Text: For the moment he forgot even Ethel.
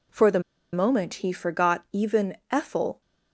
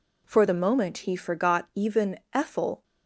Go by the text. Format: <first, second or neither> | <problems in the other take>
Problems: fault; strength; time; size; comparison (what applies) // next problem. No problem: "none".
second | pauses between "the" and "moment"; slight; at 0.4 s; 0.32 s long // pauses between "even" and "Ethel"; slight; at 2.3 s; 0.16 s long; slight in the second